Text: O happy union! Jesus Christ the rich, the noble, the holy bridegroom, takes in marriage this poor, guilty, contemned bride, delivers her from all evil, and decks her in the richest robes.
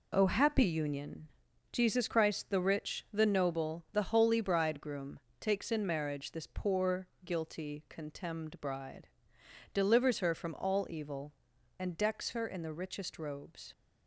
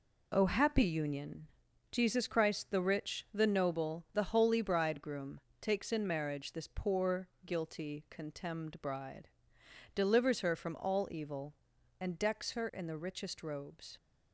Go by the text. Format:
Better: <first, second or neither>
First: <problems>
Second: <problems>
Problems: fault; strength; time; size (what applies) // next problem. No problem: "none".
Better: neither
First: none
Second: none